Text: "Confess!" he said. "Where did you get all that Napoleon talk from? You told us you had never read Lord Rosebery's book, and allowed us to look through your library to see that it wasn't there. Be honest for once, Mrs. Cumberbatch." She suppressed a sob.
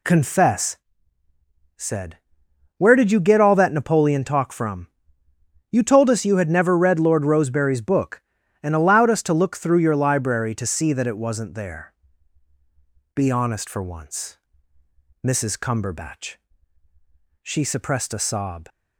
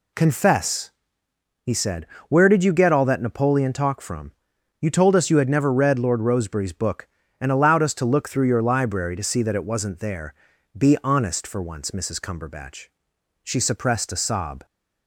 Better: second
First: skips "he"; at 1.2 s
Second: none

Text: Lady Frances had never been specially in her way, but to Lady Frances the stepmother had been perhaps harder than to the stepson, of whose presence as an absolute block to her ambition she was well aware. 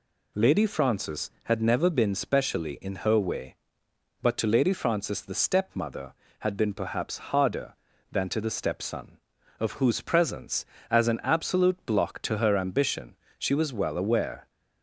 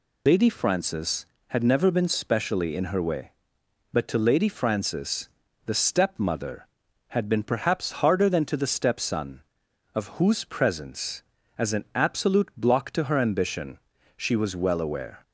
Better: first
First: pauses between "ambition" and "she"; slight; at 13.1 s; 0.24 s long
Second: loses the start of "Lady"; at 0.2 s; 85 ms // pauses between "Frances" and "the"; at 5.2 s; 0.38 s long // pauses between "ambition" and "she"; at 13.7 s; 0.38 s long

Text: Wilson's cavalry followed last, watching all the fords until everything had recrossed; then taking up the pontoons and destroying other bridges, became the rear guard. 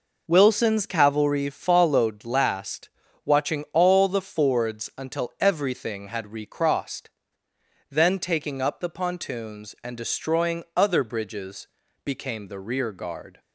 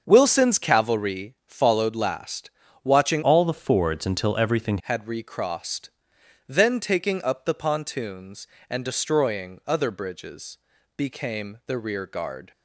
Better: first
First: none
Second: starts louder than the rest; until 1.0 s; 7 dB // changes voice from "all" to "everything"; from 3.2 to 4.7 s; 1.5 s long

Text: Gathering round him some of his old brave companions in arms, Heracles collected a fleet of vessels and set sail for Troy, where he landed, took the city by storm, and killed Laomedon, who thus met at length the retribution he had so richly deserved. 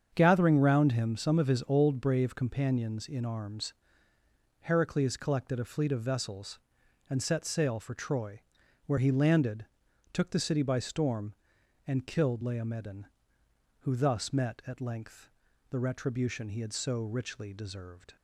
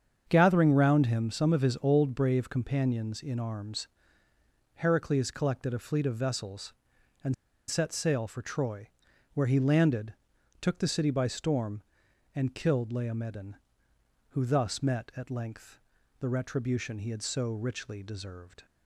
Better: first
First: starts louder than the rest; strong; until 1.1 s; 7.5 dB // pauses between "length" and "the"; at 15.2 s; 0.40 s long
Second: starts louder than the rest; strong; until 1.3 s; 7.5 dB // pauses between "and" and "set"; slight; at 7.3 s; 0.34 s long // pauses between "length" and "the"; at 15.7 s; 0.40 s long

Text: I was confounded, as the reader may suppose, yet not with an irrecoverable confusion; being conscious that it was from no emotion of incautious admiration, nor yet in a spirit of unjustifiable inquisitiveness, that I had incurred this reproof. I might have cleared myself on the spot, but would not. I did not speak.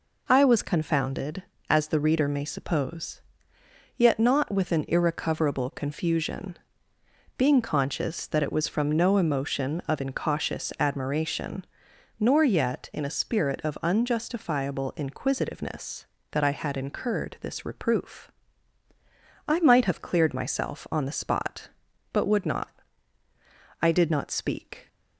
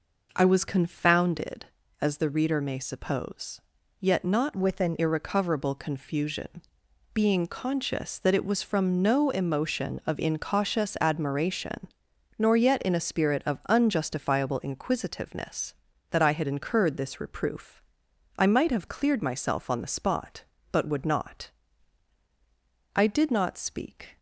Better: first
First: none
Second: changes voice from "with" to "an"; from 4.5 to 4.9 s; 0.4 s long

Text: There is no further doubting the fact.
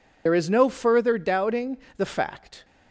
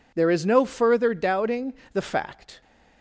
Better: second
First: loses the start of "There"; at 0.2 s; 70 ms // pauses between "doubting" and "the"; slight; at 1.7 s; 0.20 s long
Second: pauses between "doubting" and "the"; slight; at 1.7 s; 0.20 s long

